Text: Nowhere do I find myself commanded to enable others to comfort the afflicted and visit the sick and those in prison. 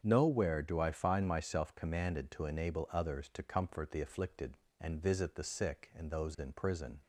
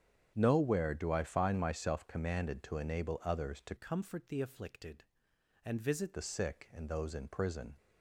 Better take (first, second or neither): first